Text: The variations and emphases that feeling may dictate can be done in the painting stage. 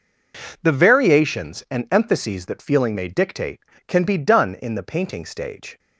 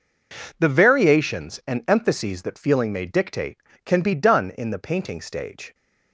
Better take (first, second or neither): neither